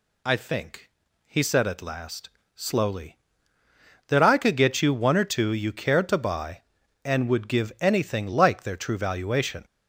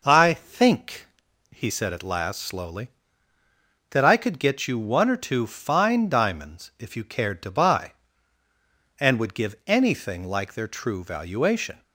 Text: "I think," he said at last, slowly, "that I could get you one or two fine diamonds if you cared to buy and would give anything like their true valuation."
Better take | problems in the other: second | skips "fine diamonds if"; at 5.5 s

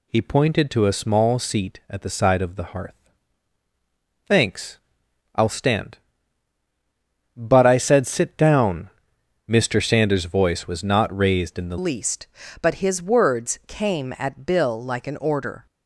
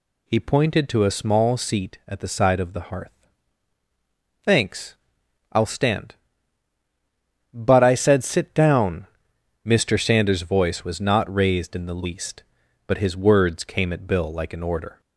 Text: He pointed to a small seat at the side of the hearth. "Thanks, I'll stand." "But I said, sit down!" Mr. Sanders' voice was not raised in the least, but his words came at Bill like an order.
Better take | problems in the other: second | changes voice at "least"; from 11.7 s on; 3.9 s long

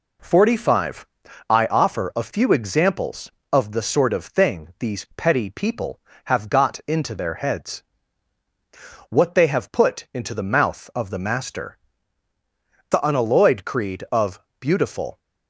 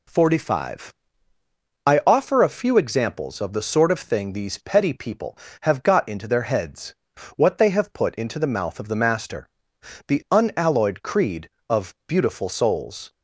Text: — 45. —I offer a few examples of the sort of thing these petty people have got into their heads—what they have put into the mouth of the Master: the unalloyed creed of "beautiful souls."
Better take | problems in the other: second | pauses between "of" and "beautiful"; slight; at 14.3 s; 0.22 s long // stops before "souls"; at 15.1 s

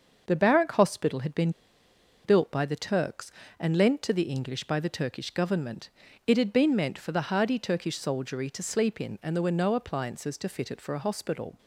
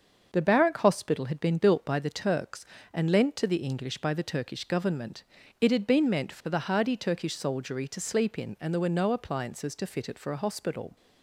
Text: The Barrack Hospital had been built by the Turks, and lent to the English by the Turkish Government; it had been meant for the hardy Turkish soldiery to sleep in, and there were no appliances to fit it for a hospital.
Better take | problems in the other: second | starts louder than the rest; until 1.2 s; 6.5 dB; also in the second // pauses between "been" and "built"; noticeable; at 1.4 s; 0.74 s long

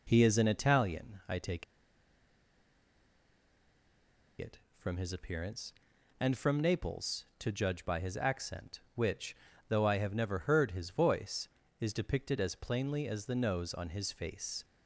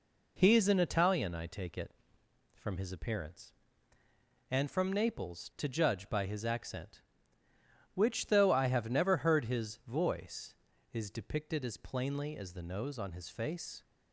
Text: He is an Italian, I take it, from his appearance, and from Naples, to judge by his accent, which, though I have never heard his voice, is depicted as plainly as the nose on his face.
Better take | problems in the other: second | pauses between "take" and "it"; strong; at 1.6 s; 2.7 s long

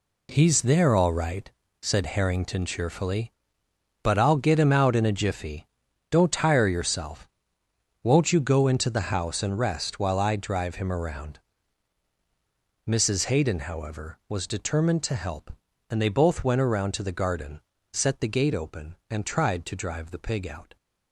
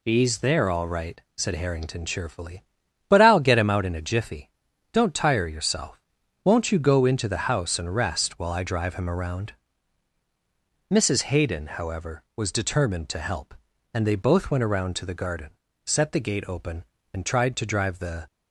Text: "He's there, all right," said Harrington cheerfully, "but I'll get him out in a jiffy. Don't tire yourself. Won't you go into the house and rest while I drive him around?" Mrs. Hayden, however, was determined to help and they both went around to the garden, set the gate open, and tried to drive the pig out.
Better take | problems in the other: first | stops before "pig out"; at 18.2 s

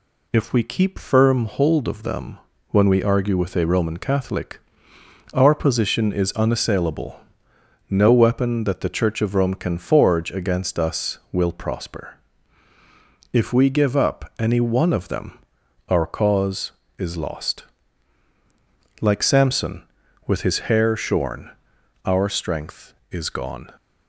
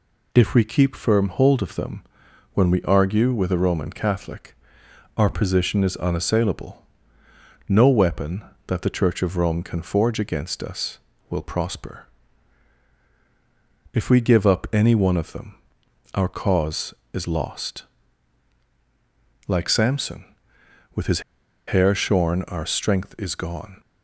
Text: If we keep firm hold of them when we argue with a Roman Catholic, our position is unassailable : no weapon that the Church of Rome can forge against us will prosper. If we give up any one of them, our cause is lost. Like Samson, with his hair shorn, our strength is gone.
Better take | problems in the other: first | pauses between "them" and "when"; noticeable; at 2.0 s; 0.50 s long; slight in the first // pauses between "his" and "hair"; noticeable; at 21.2 s; 0.46 s long

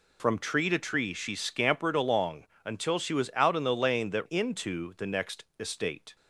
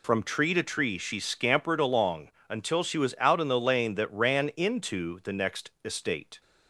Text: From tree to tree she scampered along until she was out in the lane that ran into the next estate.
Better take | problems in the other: second | pauses between "along" and "until"; slight; at 2.4 s; 0.18 s long; slight in the second // skips "ran"; at 4.2 s

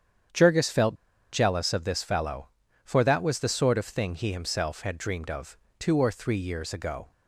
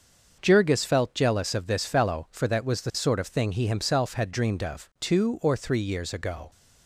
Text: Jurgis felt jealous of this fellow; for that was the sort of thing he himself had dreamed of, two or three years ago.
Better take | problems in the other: second | starts louder than the rest; strong; until 1.7 s; 8.5 dB; also in the second // pauses between "felt" and "jealous"; at 0.9 s; 0.38 s long

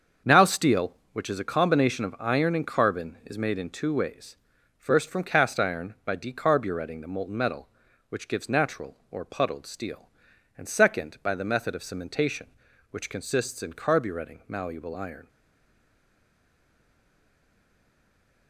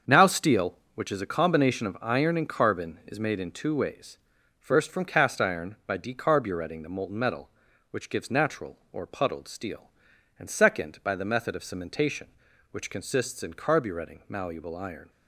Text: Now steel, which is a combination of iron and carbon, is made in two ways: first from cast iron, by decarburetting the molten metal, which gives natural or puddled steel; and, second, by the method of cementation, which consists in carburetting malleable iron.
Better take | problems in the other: second | starts louder than the rest; until 1.4 s; 7 dB; also in the second // stays silent after the last word; strong; from 15.2 s on; 3.2 s long

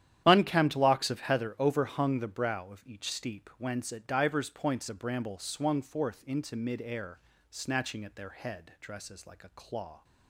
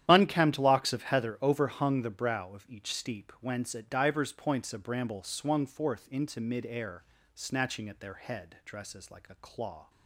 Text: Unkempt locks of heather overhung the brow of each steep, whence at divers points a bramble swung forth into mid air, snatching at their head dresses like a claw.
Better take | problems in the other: neither | starts louder than the rest; strong; the same in both

